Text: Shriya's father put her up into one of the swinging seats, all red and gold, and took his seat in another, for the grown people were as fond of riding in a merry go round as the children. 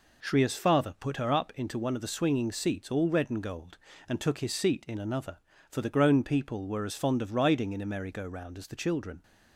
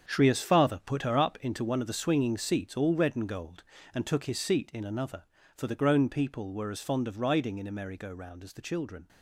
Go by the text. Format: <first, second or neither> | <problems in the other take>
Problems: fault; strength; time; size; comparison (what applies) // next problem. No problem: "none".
first | gets quieter; strong; throughout; 11.5 dB